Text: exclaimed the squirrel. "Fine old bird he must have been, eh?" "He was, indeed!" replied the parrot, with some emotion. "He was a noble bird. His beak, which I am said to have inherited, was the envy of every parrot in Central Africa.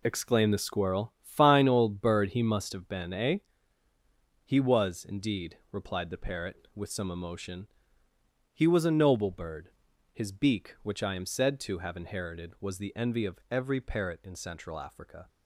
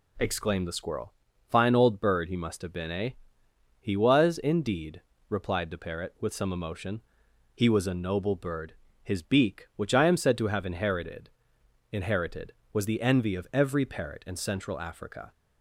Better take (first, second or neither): first